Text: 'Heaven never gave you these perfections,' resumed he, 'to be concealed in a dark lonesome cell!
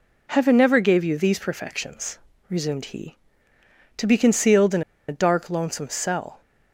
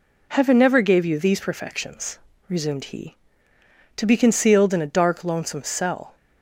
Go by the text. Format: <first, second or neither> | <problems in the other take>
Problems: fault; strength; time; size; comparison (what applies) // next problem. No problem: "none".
second | pauses between "in" and "a"; slight; at 4.8 s; 0.26 s long